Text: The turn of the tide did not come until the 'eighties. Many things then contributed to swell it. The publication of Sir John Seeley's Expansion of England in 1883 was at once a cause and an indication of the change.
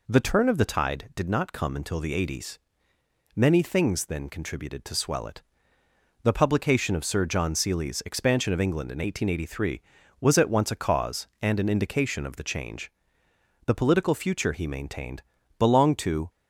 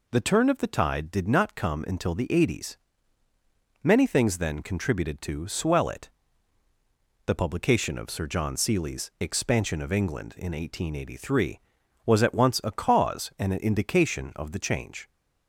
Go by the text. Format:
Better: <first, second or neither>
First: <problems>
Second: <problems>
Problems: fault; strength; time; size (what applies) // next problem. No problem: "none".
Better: second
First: goes on to say "The political future he maintained belonged to"; strong; from 13.6 s on; 2.6 s long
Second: none